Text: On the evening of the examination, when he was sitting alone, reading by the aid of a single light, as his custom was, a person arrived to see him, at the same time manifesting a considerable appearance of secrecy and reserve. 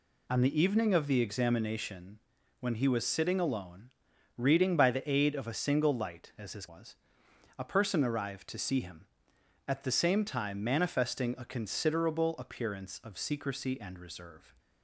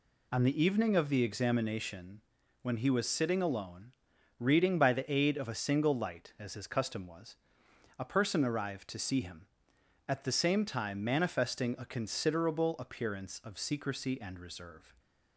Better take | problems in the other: second | skips "custom"; at 6.6 s

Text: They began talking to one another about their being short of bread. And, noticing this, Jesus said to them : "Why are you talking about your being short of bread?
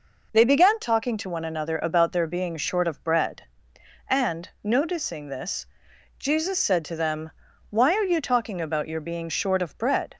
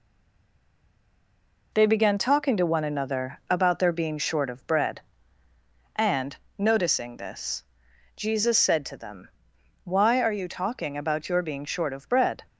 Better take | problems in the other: first | stays silent before the first word; noticeable; until 1.7 s; 1.7 s long

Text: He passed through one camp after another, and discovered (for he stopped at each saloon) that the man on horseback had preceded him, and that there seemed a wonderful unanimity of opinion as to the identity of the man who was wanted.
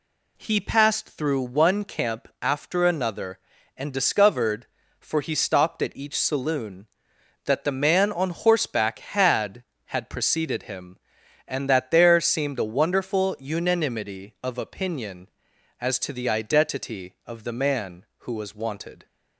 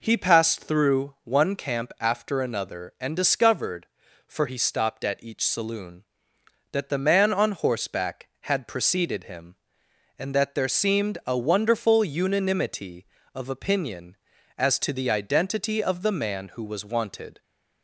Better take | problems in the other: second | says "had" twice; at 9.8 s

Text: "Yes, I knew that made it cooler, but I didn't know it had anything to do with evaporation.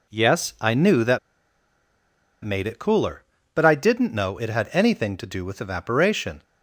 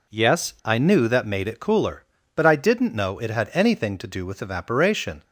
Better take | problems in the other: second | pauses between "that" and "made"; strong; at 1.1 s; 1.2 s long

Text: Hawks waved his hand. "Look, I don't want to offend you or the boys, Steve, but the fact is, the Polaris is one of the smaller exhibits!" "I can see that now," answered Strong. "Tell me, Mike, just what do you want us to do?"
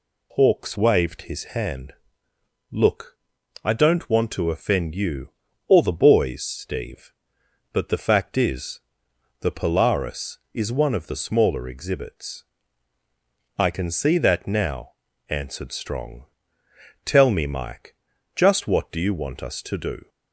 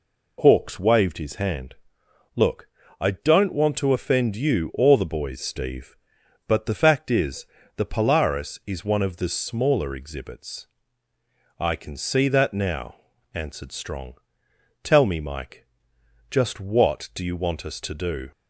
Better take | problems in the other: neither | none

